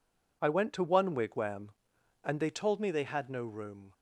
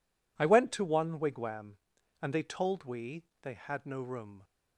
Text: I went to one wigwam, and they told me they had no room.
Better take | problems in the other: first | says "we" for "me"; at 2.8 s

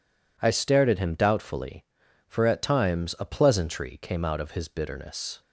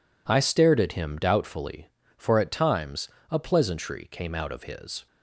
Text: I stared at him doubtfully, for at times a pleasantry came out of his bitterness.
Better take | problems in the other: first | pauses between "times" and "a"; slight; at 3.0 s; 0.24 s long // stops before "bitterness"; at 5.0 s

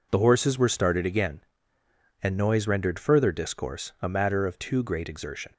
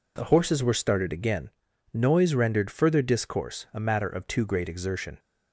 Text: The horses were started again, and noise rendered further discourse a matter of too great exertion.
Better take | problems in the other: first | skips "and"; at 1.7 s

